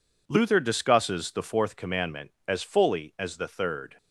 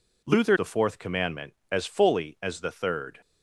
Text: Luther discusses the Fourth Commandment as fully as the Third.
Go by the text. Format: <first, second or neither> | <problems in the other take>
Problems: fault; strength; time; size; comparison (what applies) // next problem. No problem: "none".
first | skips "discusses"; at 0.5 s